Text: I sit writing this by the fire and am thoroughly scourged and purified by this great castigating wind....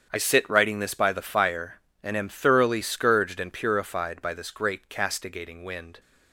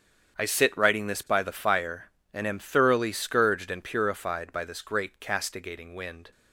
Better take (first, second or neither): neither